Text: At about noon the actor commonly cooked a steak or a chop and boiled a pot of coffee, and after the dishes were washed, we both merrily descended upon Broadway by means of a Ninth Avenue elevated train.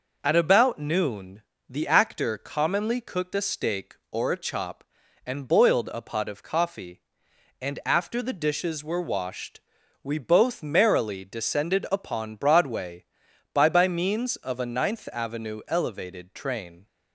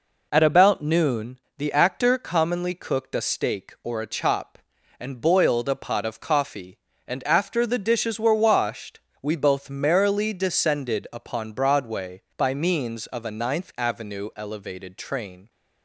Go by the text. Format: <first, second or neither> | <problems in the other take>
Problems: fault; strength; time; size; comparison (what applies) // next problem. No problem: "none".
second | pauses between "noon" and "the"; slight; at 1.4 s; 0.26 s long; slight in the second // says "by" twice; at 13.6 s